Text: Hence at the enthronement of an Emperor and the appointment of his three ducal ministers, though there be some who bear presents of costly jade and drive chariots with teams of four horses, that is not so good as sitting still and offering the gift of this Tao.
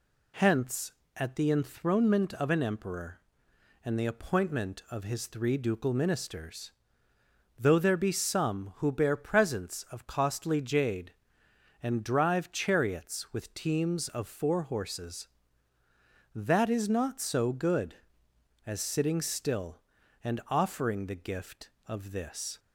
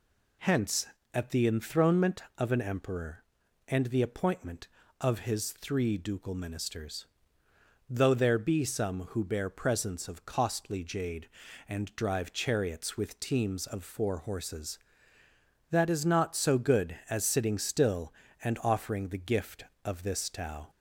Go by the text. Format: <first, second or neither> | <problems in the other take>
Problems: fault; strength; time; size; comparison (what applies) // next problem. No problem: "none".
second | stops before "Tao"; at 22.5 s